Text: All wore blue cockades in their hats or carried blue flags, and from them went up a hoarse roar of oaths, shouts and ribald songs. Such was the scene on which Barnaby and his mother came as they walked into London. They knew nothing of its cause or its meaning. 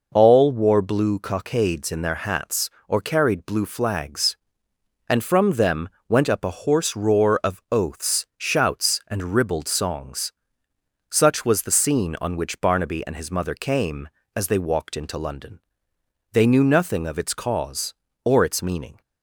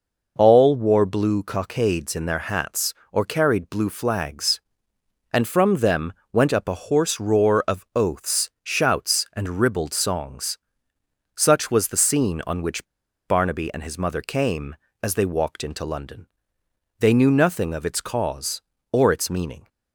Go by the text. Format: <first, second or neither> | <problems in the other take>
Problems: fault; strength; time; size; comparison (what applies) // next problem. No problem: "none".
first | pauses between "them" and "went"; slight; at 6.1 s; 0.18 s long; slight in the first // pauses between "which" and "Barnaby"; at 12.8 s; 0.42 s long